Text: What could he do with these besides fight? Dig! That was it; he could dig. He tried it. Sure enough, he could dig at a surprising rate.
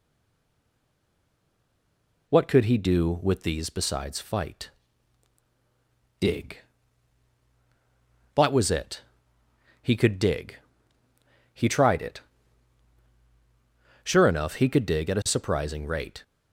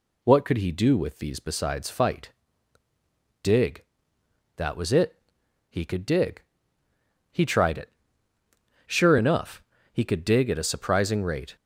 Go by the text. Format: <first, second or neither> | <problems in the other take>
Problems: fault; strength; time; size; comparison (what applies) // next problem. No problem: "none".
second | stays silent before the first word; until 2.2 s; 2.2 s long